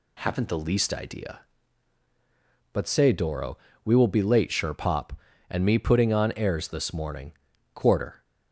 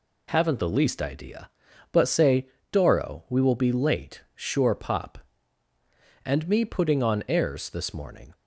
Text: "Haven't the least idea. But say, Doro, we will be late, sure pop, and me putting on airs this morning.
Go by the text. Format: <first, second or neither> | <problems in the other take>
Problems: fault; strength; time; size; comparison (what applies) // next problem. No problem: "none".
second | goes on to say "Quarter"; slight; from 7.7 s on; 0.48 s long